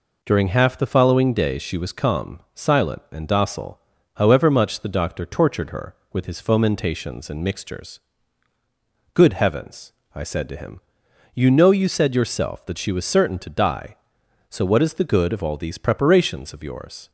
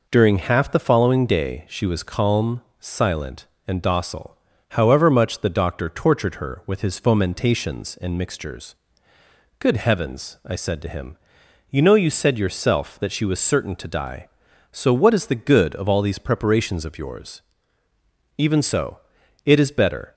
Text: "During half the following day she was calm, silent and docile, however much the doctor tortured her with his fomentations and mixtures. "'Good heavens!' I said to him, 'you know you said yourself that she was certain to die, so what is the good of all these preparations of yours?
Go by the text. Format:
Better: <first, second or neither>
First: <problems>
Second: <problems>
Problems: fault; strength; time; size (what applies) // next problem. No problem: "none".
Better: first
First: none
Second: goes on to say "Even so it is better"; strong; from 18.3 s on; 1.7 s long